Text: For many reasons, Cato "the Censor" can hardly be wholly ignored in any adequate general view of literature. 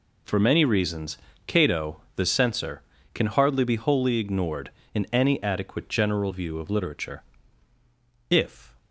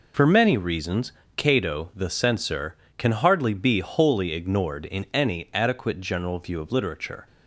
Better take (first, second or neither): second